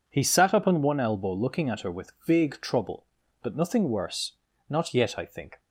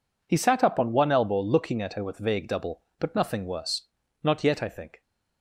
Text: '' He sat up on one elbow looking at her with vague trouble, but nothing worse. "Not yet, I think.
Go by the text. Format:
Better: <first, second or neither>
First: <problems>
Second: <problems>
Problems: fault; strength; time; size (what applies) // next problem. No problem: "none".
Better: first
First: none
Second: says "double" for "trouble"; at 2.4 s